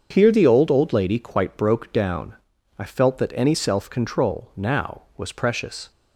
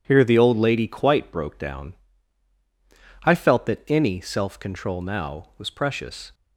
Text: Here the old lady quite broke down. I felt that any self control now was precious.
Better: second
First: starts louder than the rest; until 1.1 s; 7 dB // says "old" twice; at 0.6 s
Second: none

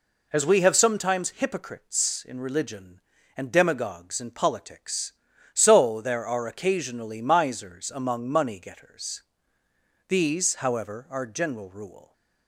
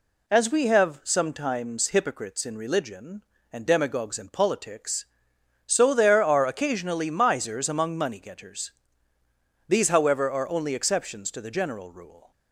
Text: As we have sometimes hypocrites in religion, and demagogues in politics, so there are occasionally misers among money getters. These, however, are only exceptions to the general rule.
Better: second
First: skips "only exceptions to the"; at 11.2 s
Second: none

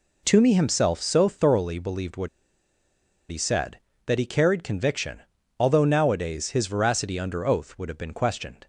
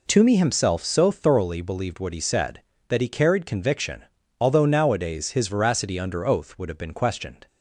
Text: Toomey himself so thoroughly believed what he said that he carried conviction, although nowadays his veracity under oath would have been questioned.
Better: second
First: pauses between "what" and "he"; at 2.2 s; 1.0 s long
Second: none

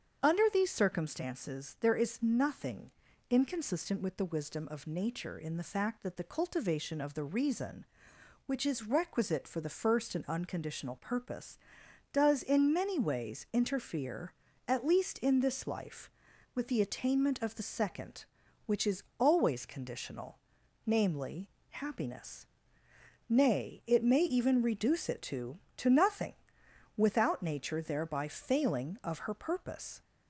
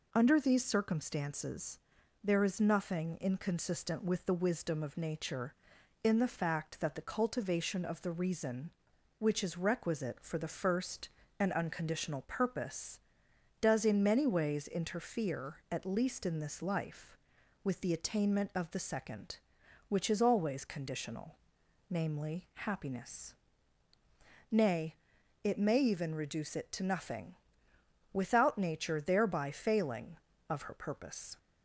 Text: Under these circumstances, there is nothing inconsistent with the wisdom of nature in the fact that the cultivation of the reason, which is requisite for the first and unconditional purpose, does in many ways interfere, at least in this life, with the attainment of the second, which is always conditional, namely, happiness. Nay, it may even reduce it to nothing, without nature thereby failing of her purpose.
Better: second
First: starts louder than the rest; strong; until 1.3 s; 7 dB // pauses between "nothing" and "inconsistent"; at 2.8 s; 0.40 s long // pauses between "is" and "always"; slight; at 19.0 s; 0.16 s long // says "to" twice; at 25.7 s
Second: none

